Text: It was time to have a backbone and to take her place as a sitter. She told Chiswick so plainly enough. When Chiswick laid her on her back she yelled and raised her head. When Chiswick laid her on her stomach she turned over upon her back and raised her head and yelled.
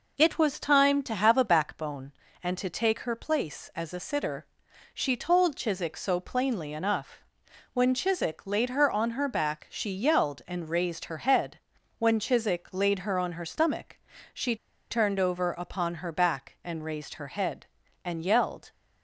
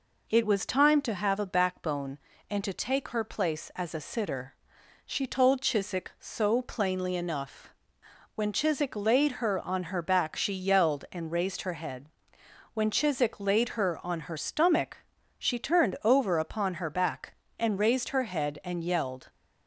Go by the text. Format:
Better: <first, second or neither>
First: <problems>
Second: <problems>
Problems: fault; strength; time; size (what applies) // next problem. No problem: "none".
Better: second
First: pauses between "stomach" and "she"; slight; at 13.9 s; 0.34 s long // pauses between "she" and "turned"; slight; at 14.5 s; 0.34 s long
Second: pauses between "stomach" and "she"; at 14.9 s; 0.40 s long